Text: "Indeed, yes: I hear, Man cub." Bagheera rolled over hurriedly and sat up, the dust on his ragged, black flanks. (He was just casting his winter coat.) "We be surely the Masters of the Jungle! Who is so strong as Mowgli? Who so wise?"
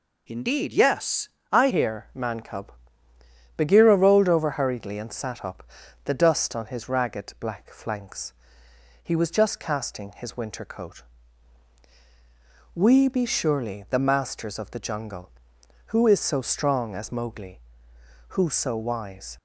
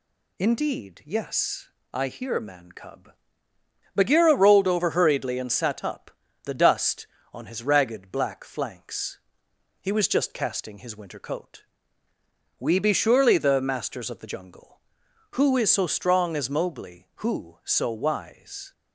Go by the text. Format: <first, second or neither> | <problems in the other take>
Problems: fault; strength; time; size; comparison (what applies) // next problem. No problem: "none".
second | changes voice at "hear"; from 1.6 s on; 17.7 s long